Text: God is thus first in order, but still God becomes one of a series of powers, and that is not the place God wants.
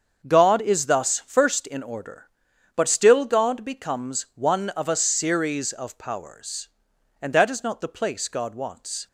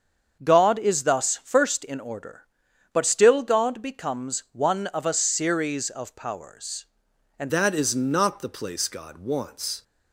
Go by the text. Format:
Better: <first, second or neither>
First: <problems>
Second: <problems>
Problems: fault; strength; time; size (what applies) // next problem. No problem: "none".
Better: first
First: starts louder than the rest; until 1.3 s; 7 dB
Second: starts louder than the rest; until 1.4 s; 7 dB // changes voice at "that"; from 7.5 s on; 2.3 s long